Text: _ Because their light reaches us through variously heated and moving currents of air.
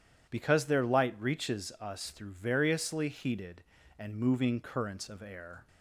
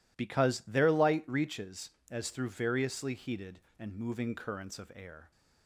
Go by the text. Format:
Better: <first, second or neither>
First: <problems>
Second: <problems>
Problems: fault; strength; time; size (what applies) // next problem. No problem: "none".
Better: first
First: none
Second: says "as" for "us"; at 2.0 s